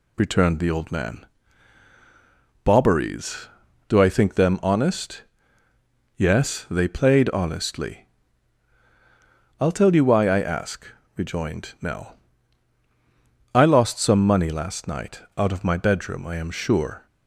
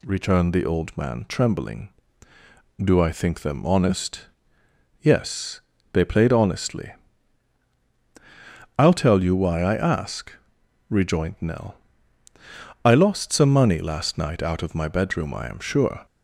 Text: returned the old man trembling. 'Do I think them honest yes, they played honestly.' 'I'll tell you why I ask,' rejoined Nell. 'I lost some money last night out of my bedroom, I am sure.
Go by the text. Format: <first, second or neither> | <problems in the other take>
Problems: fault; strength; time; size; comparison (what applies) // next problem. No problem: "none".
second | says "bobberies" for "trembling"; at 2.6 s // pauses between "honest" and "yes"; noticeable; at 5.2 s; 0.94 s long; noticeable in the second